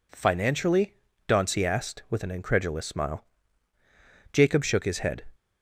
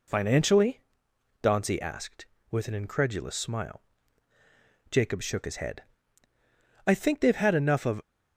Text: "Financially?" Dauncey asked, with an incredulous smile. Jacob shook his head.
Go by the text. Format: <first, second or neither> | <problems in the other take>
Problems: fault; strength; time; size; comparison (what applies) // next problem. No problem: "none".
first | goes on to say "I think they've had enough of"; noticeable; from 6.8 s on; 1.1 s long